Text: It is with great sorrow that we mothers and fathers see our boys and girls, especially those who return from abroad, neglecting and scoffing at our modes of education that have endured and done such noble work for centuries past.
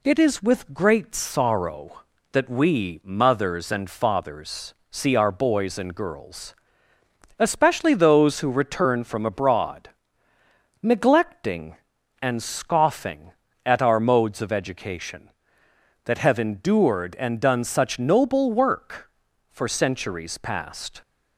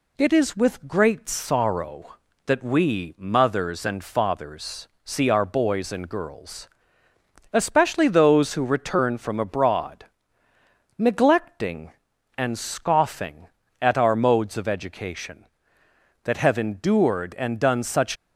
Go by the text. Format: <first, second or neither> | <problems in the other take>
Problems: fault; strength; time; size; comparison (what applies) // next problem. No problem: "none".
first | pauses between "fathers" and "see"; slight; at 4.8 s; 0.16 s long; slight in the first // stops before "noble work for centuries past"; at 18.1 s